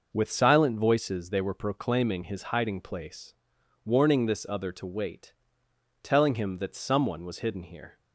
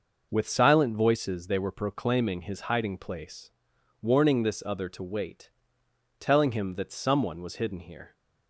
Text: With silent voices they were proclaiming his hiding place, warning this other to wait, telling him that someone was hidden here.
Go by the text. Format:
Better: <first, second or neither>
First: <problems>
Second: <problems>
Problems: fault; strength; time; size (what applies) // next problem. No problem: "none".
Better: neither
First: none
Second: none